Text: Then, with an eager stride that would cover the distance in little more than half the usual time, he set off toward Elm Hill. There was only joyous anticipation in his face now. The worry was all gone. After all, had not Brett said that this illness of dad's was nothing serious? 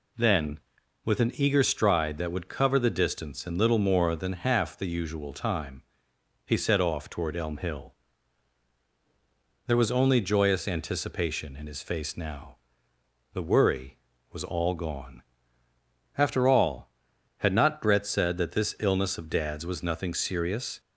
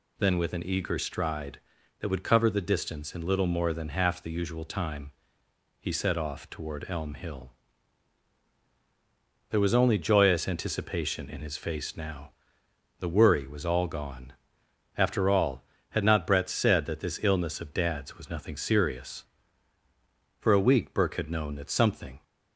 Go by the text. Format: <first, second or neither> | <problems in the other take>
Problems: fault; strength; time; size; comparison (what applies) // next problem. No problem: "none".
first | goes on to say "For a week Burke had known that something"; strong; from 20.3 s on; 1.8 s long